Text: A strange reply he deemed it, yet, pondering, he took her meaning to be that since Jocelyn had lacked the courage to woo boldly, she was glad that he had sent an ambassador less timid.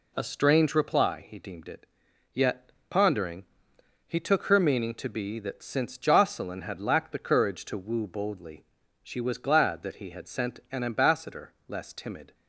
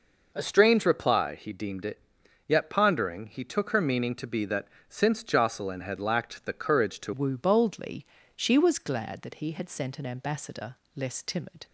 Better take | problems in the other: first | pauses between "that" and "since"; slight; at 4.6 s; 0.22 s long // changes voice at "woo"; from 7.1 s on; 4.5 s long // pauses between "ambassador" and "less"; slight; at 10.7 s; 0.20 s long

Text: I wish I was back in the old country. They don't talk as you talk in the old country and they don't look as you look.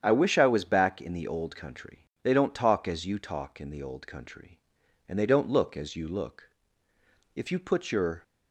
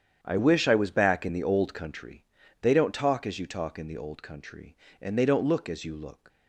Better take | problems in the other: second | starts louder than the rest; strong; until 1.0 s; 8.5 dB; strong in the second // goes on to say "If you put your"; noticeable; from 7.3 s on; 0.88 s long

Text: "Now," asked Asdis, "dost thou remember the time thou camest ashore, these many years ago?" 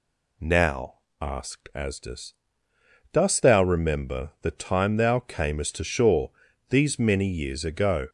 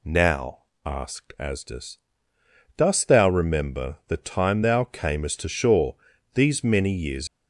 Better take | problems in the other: first | stops before "ago"; at 7.2 s

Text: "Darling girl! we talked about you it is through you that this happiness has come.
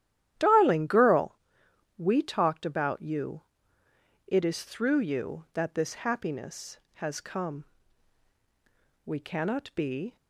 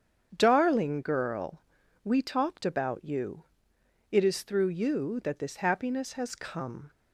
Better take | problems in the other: second | starts louder than the rest; strong; until 1.3 s; 11.5 dB; strong in the second // pauses between "you" and "it"; noticeable; at 3.4 s; 0.84 s long; noticeable in the second // goes on to say "We cannot be"; noticeable; from 9.0 s on; 1.1 s long

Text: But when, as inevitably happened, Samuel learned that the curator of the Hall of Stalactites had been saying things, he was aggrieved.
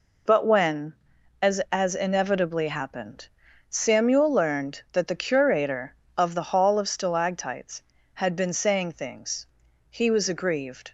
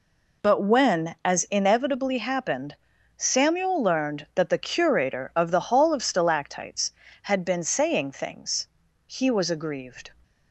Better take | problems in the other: second | says "as" twice; at 1.7 s

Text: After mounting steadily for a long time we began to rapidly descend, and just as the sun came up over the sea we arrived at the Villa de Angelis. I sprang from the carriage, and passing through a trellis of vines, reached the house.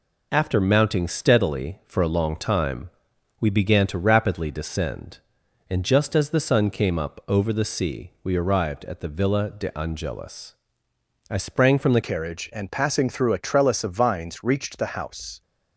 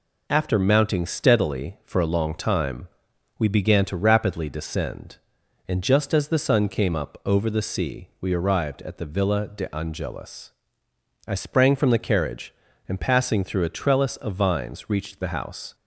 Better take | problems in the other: second | pauses between "time" and "we"; noticeable; at 2.8 s; 0.48 s long; noticeable in the second // changes voice at "carriage"; from 12.0 s on; 3.4 s long

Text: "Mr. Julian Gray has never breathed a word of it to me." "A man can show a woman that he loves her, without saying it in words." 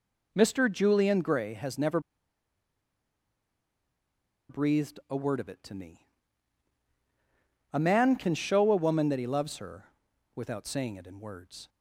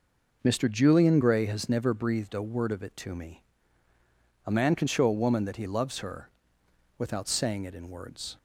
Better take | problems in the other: second | pauses between "never" and "breathed"; strong; at 1.9 s; 2.4 s long

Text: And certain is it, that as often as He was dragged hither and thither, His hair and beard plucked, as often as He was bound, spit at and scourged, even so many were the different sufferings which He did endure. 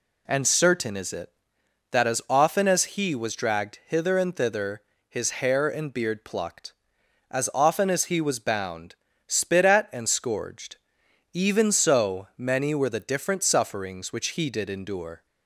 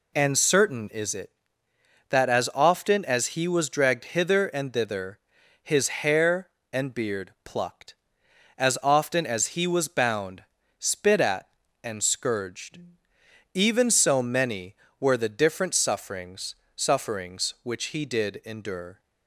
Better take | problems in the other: first | says "sufferings" twice; at 16.7 s

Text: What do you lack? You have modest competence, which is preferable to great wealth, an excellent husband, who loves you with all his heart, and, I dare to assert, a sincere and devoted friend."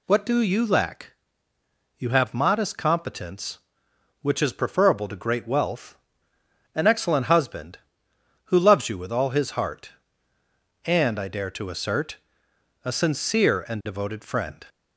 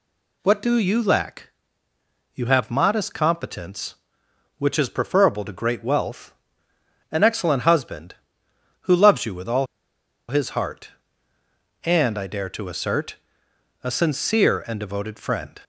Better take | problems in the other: first | pauses between "all" and "his"; noticeable; at 9.6 s; 0.62 s long

